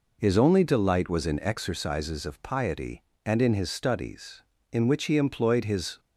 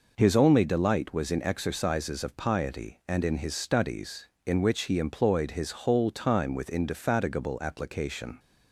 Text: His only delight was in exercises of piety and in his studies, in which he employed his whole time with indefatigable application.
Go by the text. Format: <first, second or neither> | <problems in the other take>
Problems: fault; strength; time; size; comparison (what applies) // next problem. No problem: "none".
second | stops before "whole time with indefatigable application"; at 5.9 s